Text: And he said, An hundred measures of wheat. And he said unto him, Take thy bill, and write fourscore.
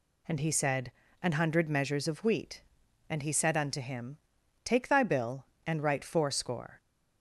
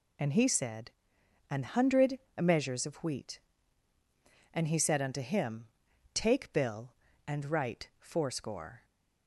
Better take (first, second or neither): first